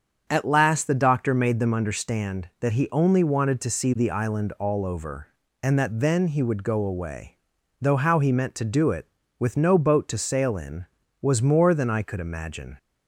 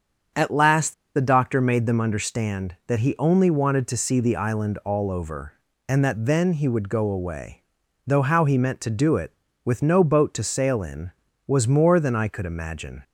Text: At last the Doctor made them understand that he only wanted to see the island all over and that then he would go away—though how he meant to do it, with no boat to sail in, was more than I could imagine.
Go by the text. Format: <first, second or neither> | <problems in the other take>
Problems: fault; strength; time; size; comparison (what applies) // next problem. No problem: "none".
first | starts louder than the rest; strong; until 1.5 s; 7.5 dB; strong in the first // pauses between "last" and "the"; slight; at 0.9 s; 0.22 s long